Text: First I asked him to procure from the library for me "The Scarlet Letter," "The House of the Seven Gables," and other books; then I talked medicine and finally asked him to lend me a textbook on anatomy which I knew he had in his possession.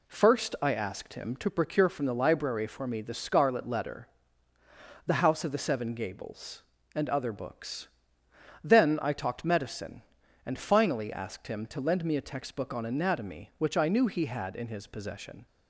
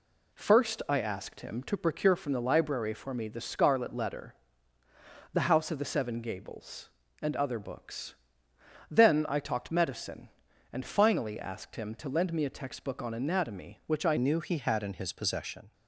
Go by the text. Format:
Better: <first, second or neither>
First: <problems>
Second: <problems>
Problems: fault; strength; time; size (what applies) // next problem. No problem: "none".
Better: first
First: none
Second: changes voice at "knew"; from 14.1 s on; 1.6 s long